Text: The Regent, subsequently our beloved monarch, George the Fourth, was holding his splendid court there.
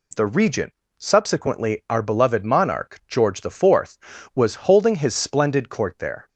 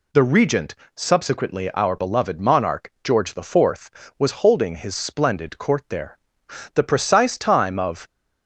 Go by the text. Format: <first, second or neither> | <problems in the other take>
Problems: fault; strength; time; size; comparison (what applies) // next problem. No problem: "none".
first | goes on to say "The precise time of"; from 6.7 s on; 1.3 s long